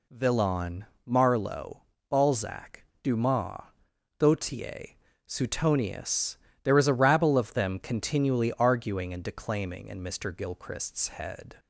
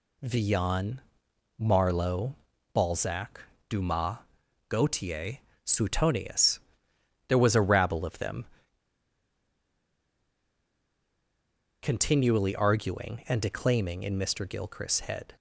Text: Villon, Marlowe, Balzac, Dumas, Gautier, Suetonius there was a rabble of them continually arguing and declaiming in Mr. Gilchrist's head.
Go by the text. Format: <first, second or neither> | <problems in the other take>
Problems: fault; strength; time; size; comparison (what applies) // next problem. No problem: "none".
first | pauses between "Suetonius" and "there"; noticeable; at 6.5 s; 0.70 s long; slight in the first // pauses between "them" and "continually"; strong; at 8.4 s; 3.3 s long